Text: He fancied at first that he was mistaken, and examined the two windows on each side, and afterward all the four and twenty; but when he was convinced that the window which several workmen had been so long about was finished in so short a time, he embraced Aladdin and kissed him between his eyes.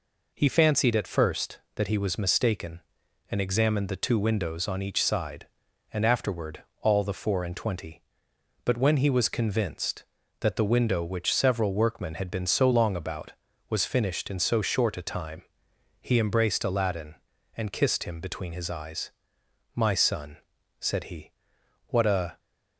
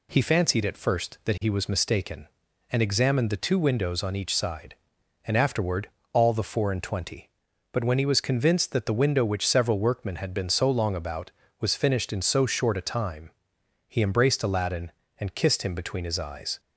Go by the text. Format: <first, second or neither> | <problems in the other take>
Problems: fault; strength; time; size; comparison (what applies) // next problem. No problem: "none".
second | pauses between "afterward" and "all"; slight; at 6.6 s; 0.18 s long; slight in the second // goes on to say "My son said he what a"; strong; from 19.7 s on; 2.6 s long